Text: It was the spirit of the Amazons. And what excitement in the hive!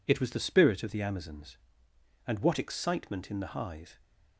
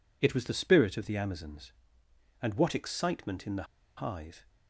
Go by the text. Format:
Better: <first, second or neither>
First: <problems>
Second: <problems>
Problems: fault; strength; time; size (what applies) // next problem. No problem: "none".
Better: first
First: none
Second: pauses between "the" and "hive"; slight; at 3.6 s; 0.33 s long